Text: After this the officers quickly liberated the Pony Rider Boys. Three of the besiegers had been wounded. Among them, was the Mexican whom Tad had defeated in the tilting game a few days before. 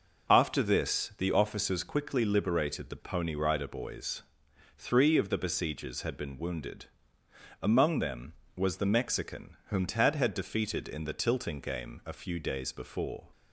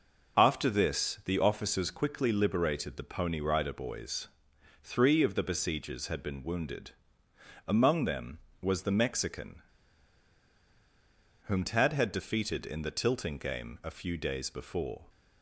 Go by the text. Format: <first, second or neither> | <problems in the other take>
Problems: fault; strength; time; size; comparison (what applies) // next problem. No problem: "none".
first | pauses between "Mexican" and "whom"; strong; at 9.6 s; 1.8 s long